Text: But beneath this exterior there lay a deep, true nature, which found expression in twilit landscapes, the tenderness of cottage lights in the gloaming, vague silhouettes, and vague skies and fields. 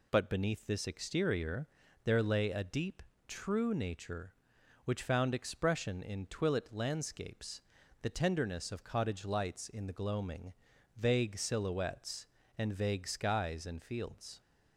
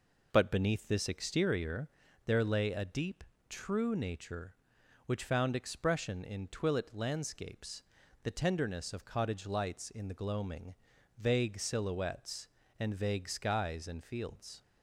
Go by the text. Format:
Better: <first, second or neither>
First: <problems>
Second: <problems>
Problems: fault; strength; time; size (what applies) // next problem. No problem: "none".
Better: first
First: pauses between "exterior" and "there"; at 1.6 s; 0.38 s long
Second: starts louder than the rest; noticeable; until 1.5 s; 4.5 dB // pauses between "exterior" and "there"; at 1.8 s; 0.38 s long